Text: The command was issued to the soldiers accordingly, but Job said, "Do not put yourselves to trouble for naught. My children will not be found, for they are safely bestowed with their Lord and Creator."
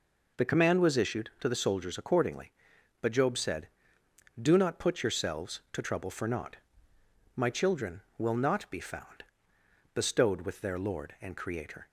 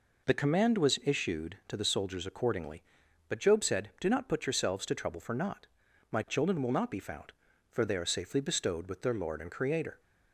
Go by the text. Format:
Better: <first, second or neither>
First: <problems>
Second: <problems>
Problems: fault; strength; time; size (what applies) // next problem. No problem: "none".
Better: second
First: skips "for they are safely"; at 9.5 s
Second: none